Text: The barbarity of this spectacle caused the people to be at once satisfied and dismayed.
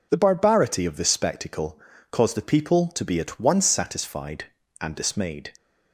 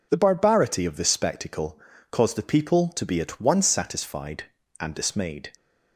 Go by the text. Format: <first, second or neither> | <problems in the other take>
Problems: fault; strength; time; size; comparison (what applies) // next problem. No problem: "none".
neither | pauses between "spectacle" and "caused"; slight; the same in both